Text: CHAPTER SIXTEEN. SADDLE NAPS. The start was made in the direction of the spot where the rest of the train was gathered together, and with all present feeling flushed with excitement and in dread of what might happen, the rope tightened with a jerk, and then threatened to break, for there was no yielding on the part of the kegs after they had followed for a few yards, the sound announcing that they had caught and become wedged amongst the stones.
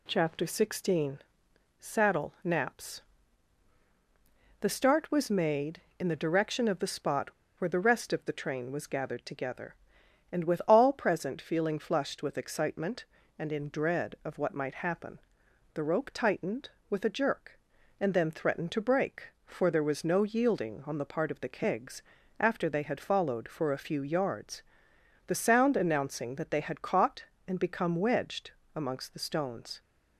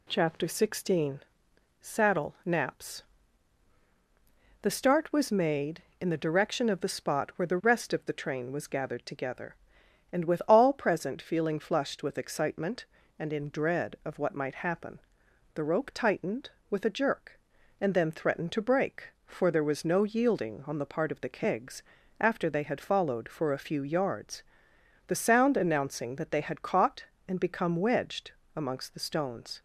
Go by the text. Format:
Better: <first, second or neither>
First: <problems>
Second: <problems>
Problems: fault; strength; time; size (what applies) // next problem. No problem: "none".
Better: second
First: pauses between "spot" and "where"; slight; at 7.2 s; 0.29 s long // pauses between "kegs" and "after"; slight; at 22.0 s; 0.36 s long // pauses between "wedged" and "amongst"; slight; at 28.5 s; 0.24 s long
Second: pauses between "kegs" and "after"; slight; at 21.8 s; 0.36 s long // pauses between "wedged" and "amongst"; slight; at 28.3 s; 0.24 s long